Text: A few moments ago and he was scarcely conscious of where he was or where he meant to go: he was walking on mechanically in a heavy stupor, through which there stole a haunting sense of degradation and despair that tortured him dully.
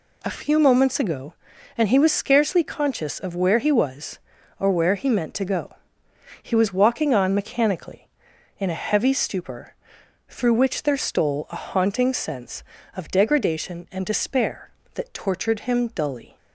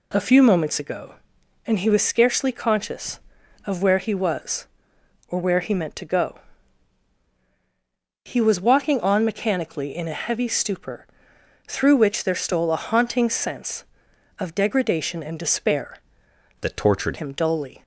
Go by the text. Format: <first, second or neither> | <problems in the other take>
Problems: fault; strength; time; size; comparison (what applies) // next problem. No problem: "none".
first | changes voice from "that" to "tortured"; from 16.6 to 17.1 s; 0.5 s long